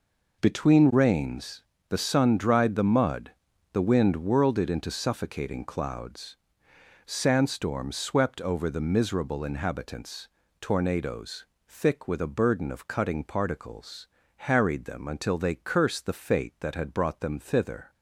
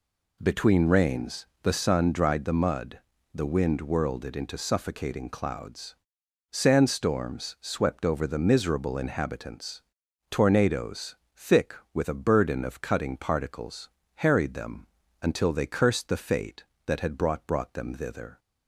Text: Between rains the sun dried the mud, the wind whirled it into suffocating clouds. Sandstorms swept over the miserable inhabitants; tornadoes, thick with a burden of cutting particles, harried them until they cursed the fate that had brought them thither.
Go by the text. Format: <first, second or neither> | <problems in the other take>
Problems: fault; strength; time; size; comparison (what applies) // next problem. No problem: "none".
first | pauses between "rains" and "the"; slight; at 1.4 s; 0.18 s long; slight in the first // pauses between "them" and "until"; slight; at 14.8 s; 0.36 s long // says "brought" twice; at 17.4 s